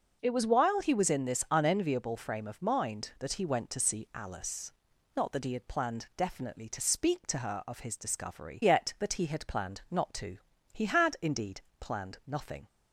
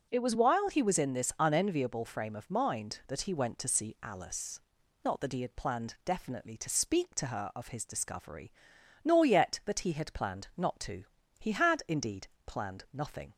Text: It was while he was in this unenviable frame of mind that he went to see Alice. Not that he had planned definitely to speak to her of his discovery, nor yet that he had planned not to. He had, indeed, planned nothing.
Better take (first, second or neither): second